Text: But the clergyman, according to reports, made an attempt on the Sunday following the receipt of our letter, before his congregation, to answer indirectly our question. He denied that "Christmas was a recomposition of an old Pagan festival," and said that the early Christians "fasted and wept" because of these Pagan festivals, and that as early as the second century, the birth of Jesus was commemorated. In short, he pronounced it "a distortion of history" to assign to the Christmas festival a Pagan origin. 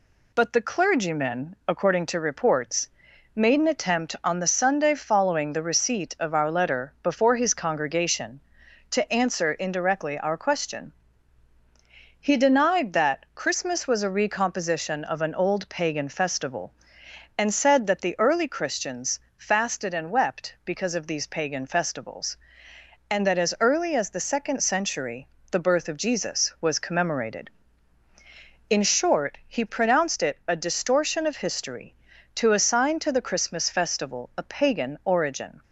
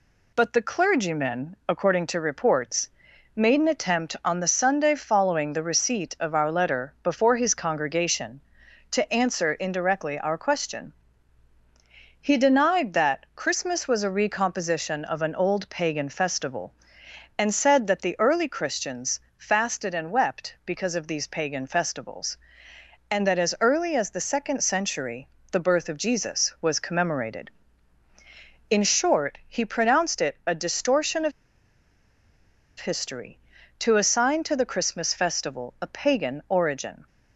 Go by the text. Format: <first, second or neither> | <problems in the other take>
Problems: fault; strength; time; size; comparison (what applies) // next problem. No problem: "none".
first | pauses between "Christians" and "fasted"; slight; at 19.1 s; 0.18 s long; slight in the first // pauses between "of" and "history"; strong; at 31.3 s; 1.4 s long